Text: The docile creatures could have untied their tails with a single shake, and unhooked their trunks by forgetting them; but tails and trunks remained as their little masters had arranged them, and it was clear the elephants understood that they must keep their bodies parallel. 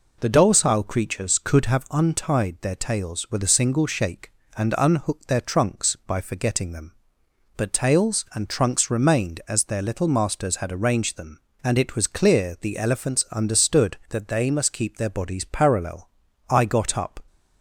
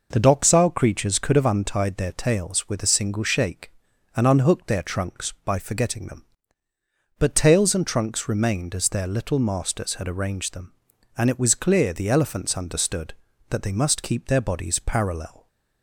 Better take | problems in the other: second | goes on to say "I got up"; noticeable; from 16.4 s on; 0.68 s long

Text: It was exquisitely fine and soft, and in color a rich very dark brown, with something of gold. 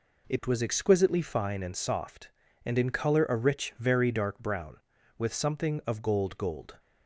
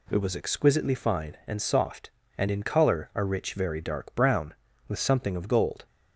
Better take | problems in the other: second | says "gold" twice; at 6.3 s

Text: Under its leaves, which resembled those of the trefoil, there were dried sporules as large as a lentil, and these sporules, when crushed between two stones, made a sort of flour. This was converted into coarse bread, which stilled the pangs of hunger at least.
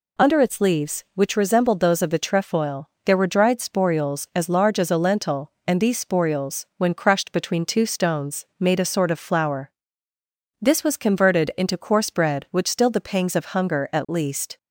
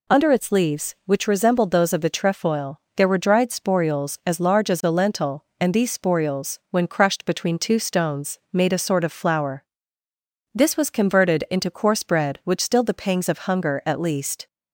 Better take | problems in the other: neither | none

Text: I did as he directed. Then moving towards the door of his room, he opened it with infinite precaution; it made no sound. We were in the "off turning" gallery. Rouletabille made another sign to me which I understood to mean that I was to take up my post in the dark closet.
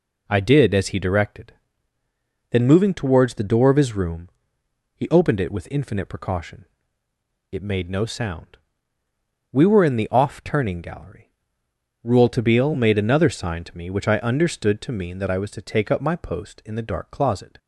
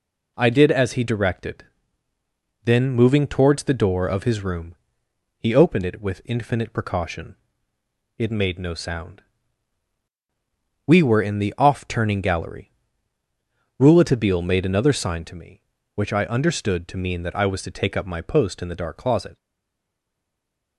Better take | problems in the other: first | stays silent after the last word; noticeable; from 19.3 s on; 1.4 s long

